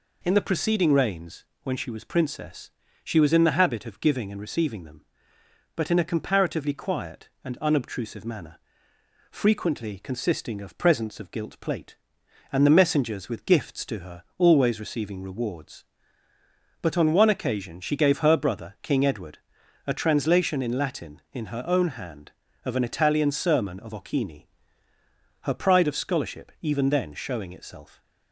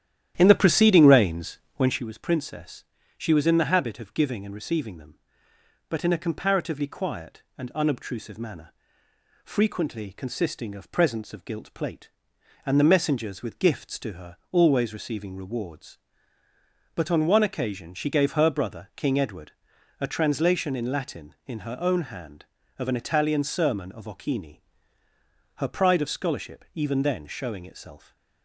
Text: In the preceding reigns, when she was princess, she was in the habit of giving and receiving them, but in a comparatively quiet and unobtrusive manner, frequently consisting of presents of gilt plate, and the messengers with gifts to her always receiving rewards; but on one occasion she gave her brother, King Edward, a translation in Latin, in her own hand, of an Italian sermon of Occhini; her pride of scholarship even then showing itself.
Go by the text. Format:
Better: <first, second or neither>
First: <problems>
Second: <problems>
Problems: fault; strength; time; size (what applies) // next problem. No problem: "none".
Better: first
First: pauses between "her" and "always"; slight; at 14.2 s; 0.16 s long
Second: starts louder than the rest; strong; until 2.1 s; 11 dB // pauses between "her" and "always"; slight; at 14.3 s; 0.16 s long